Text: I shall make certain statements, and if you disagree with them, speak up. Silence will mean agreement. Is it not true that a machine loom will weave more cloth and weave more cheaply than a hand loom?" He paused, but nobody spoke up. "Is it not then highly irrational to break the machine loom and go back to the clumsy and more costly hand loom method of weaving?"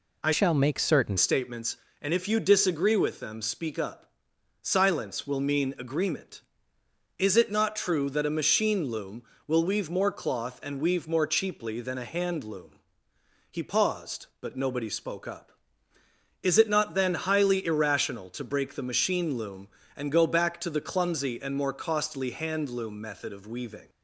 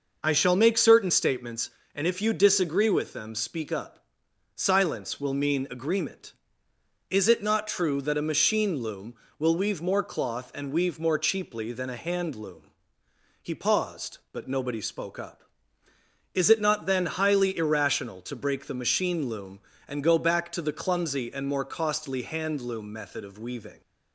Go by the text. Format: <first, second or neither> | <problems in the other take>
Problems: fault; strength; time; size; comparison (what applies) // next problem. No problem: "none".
second | changes voice from "shall" to "certain"; from 0.3 to 1.1 s; 0.8 s long